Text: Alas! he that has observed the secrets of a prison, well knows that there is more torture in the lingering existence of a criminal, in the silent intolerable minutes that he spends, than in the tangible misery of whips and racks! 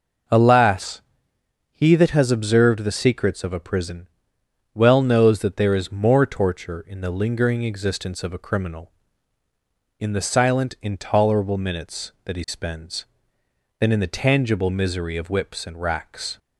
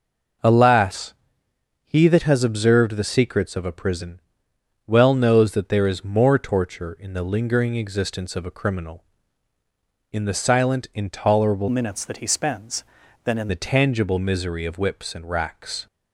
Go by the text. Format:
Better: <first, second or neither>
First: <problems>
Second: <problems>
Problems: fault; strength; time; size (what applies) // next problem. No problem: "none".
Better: first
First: none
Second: changes voice from "minutes" to "in"; from 11.6 to 13.4 s; 1.8 s long